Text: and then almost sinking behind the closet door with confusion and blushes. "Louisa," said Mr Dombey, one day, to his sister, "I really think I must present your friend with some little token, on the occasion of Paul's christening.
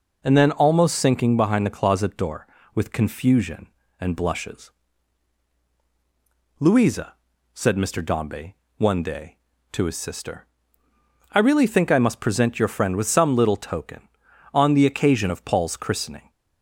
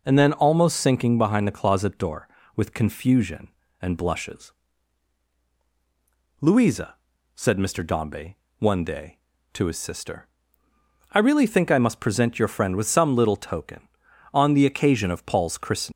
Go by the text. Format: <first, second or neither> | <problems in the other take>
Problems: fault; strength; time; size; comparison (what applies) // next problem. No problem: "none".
first | leaves "christening" unfinished; at 15.9 s; 190 ms